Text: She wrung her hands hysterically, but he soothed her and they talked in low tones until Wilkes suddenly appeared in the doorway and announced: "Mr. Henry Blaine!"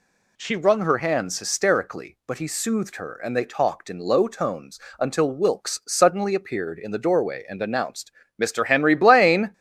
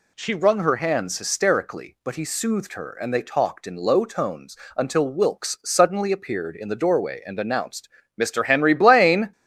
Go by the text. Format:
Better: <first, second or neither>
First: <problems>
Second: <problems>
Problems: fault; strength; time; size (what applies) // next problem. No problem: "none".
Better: neither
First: pauses between "tones" and "until"; slight; at 4.8 s; 0.18 s long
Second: pauses between "tones" and "until"; slight; at 4.5 s; 0.18 s long